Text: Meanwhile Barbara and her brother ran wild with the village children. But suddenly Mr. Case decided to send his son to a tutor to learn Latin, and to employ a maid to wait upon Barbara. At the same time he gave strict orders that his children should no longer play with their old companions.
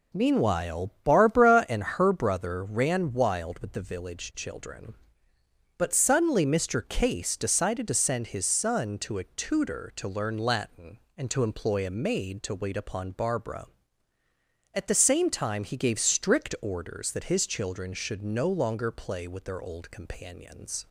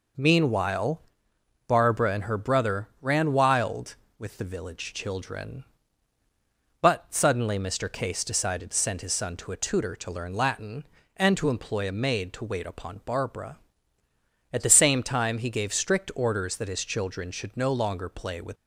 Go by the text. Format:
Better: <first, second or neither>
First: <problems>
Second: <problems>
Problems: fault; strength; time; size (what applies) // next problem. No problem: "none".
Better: first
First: none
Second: pauses between "Meanwhile" and "Barbara"; noticeable; at 1.0 s; 0.66 s long // stops before "their old companions"; at 18.5 s